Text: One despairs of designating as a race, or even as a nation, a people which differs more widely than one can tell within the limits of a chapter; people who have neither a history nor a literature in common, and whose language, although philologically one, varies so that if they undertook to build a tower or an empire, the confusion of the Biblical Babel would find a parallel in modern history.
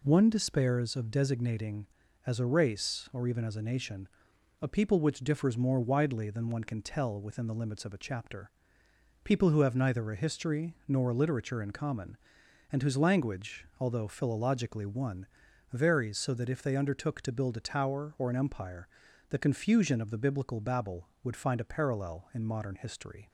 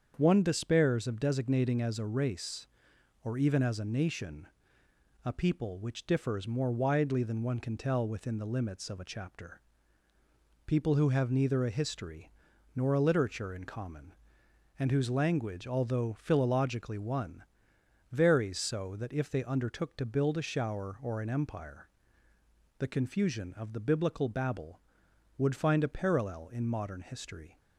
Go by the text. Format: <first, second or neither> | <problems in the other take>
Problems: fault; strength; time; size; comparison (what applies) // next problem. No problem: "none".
first | starts louder than the rest; strong; until 1.1 s; 7.5 dB // pauses between "history" and "nor"; noticeable; at 12.3 s; 0.46 s long // says "shower" for "tower"; at 20.4 s